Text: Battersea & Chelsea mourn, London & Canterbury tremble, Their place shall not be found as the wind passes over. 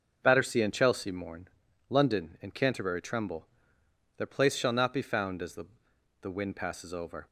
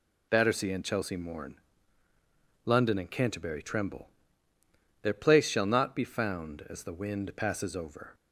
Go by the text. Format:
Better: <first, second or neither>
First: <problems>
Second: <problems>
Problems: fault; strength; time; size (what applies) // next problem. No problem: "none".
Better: second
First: says "the" twice; at 6.2 s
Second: none